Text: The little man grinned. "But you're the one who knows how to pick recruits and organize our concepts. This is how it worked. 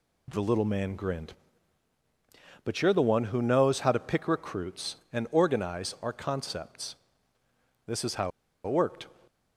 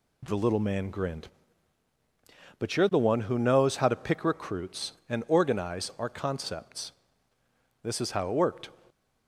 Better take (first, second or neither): second